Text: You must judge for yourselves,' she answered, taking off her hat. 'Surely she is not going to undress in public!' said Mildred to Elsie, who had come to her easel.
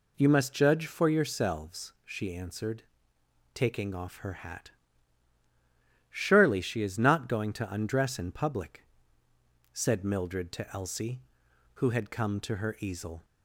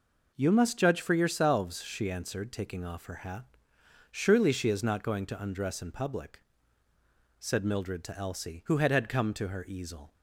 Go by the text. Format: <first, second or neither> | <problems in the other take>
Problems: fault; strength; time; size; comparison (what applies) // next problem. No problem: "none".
first | says "had" twice; at 8.9 s